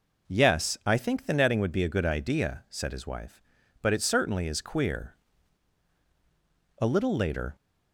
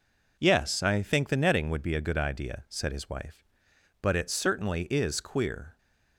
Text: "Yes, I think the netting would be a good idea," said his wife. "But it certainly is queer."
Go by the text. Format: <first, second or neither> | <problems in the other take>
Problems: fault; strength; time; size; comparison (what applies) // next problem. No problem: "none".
second | goes on to say "A little later"; noticeable; from 6.8 s on; 0.74 s long